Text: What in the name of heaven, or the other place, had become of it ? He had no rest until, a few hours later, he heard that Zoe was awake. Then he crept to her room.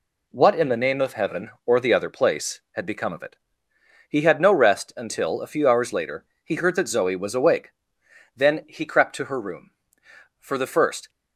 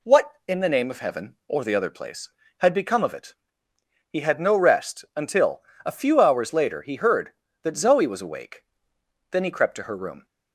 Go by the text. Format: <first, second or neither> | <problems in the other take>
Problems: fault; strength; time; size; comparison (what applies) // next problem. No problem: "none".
second | goes on to say "For the first"; noticeable; from 10.3 s on; 0.70 s long